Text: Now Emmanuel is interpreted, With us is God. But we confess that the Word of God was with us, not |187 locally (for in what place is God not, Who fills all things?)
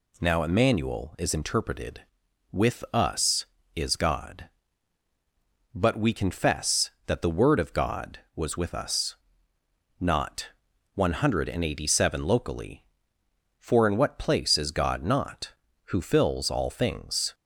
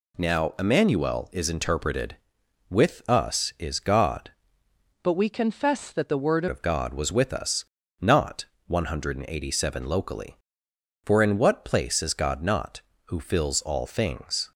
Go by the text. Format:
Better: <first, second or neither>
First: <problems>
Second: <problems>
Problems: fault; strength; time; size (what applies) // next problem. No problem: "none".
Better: first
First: none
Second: changes voice from "But" to "Word"; from 5.0 to 6.4 s; 1.4 s long